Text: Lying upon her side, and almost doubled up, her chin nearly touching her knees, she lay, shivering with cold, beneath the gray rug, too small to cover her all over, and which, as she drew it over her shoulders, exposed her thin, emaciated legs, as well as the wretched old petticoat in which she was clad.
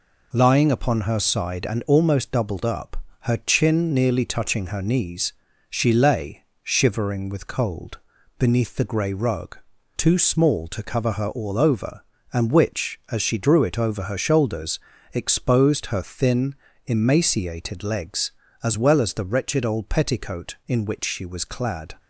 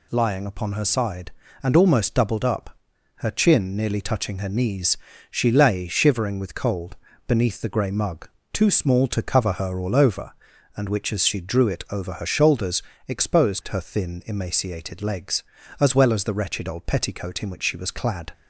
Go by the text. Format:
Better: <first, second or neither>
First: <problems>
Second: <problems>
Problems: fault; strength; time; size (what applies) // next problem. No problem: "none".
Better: first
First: none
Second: says "mug" for "rug"; at 7.9 s